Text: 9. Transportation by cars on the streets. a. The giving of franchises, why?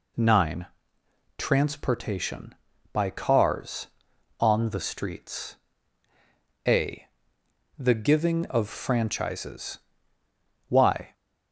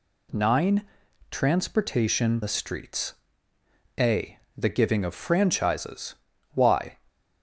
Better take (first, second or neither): first